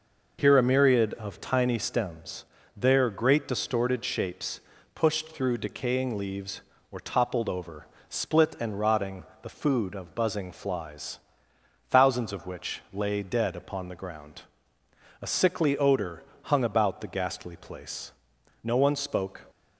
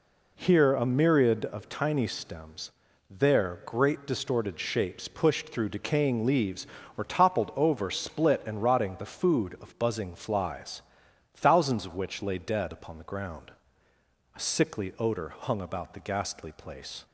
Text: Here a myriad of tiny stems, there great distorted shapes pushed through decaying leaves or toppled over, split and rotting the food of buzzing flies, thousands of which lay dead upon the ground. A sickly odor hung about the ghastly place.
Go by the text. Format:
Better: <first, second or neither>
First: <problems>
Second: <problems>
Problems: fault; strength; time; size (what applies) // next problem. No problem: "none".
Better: second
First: pauses between "shapes" and "pushed"; slight; at 4.6 s; 0.32 s long // pauses between "rotting" and "the"; slight; at 9.2 s; 0.18 s long // pauses between "odor" and "hung"; slight; at 16.2 s; 0.20 s long // goes on to say "No one spoke"; noticeable; from 18.6 s on; 0.78 s long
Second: none